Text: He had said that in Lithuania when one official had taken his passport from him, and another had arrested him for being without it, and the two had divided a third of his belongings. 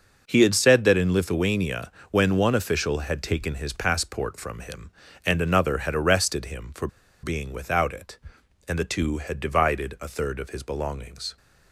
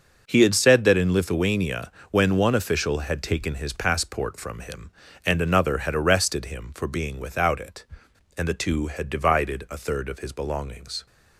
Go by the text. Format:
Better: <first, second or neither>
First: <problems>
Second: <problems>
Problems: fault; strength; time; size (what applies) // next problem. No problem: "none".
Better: second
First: pauses between "Lithuania" and "when"; slight; at 1.9 s; 0.18 s long // pauses between "for" and "being"; slight; at 6.8 s; 0.35 s long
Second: pauses between "Lithuania" and "when"; slight; at 1.9 s; 0.18 s long